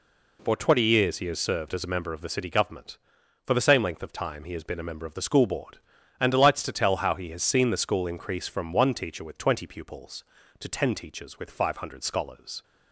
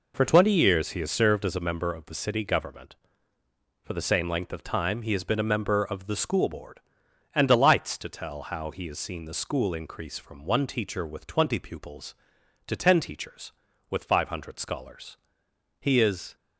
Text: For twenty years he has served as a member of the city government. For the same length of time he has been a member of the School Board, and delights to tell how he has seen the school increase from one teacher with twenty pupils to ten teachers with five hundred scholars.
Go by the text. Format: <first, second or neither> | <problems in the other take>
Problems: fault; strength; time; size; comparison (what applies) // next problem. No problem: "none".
first | goes on to say "He is"; from 15.8 s on; 0.54 s long